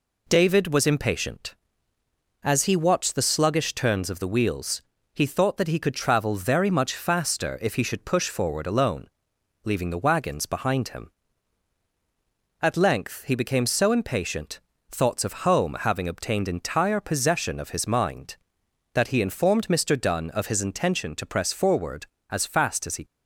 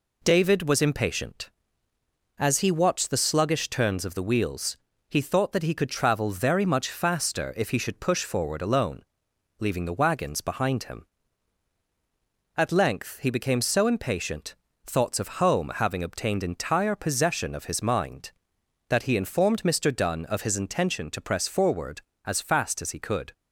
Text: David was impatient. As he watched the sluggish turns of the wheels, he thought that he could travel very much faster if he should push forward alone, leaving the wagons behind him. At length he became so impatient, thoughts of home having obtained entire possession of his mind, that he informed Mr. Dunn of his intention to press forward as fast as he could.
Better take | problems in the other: second | stops before "could"; at 23.0 s

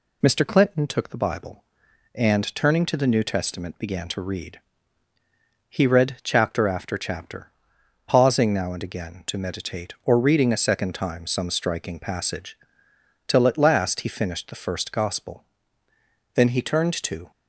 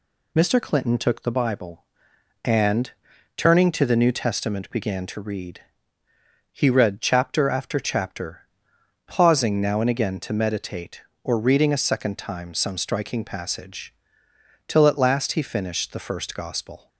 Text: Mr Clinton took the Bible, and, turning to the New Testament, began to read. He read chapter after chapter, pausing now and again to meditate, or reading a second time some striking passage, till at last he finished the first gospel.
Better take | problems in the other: second | goes on to say "Then he turned to"; noticeable; from 16.3 s on; 0.96 s long

